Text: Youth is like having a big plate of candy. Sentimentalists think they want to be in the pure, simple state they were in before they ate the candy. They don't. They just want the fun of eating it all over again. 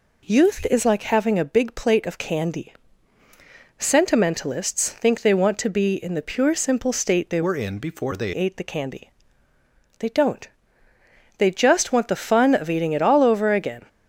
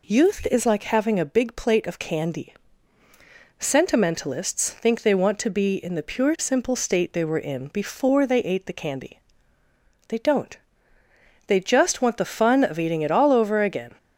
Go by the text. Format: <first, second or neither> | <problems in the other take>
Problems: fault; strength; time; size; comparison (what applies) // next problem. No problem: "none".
second | changes voice from "were" to "they"; from 7.4 to 8.3 s; 0.9 s long